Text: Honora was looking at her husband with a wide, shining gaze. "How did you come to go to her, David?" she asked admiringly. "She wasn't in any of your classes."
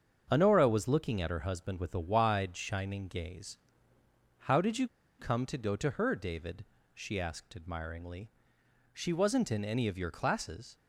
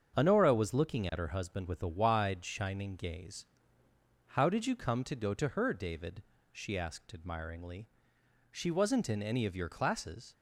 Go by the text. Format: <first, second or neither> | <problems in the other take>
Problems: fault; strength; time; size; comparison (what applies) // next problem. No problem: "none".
second | starts louder than the rest; until 1.3 s; 7 dB; also in the second // pauses between "you" and "come"; slight; at 4.8 s; 0.32 s long